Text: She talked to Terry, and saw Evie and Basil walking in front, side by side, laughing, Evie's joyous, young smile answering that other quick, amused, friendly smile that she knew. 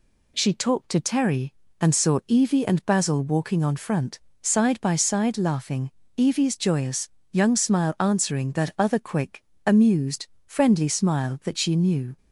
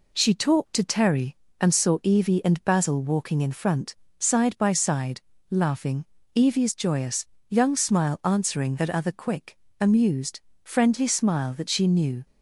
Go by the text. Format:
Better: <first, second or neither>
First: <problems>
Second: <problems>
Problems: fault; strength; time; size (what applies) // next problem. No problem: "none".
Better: second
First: says "on" for "in"; at 3.6 s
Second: none